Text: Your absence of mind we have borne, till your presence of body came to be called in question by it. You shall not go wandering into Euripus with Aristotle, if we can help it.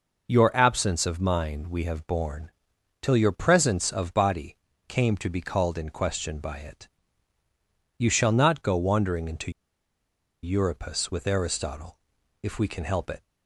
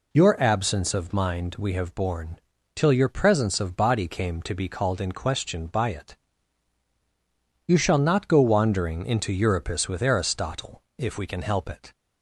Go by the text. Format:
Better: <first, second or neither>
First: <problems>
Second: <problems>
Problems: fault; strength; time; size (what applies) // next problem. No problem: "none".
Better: second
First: pauses between "body" and "came"; slight; at 4.5 s; 0.32 s long // pauses between "into" and "Euripus"; noticeable; at 9.5 s; 0.91 s long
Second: none